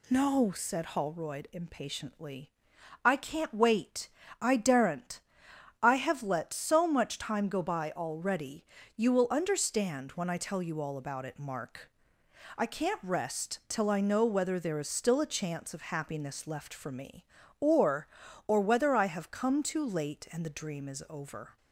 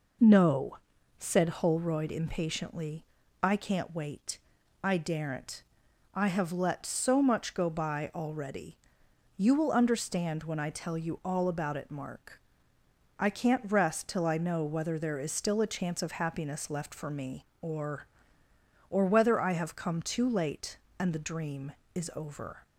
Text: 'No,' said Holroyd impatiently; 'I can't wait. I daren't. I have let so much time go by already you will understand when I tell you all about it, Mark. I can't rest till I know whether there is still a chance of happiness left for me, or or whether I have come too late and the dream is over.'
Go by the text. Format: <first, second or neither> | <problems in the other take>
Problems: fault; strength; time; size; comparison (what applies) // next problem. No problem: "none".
first | skips "time"; at 7.5 s // pauses between "already" and "you"; noticeable; at 8.7 s; 0.64 s long; slight in the first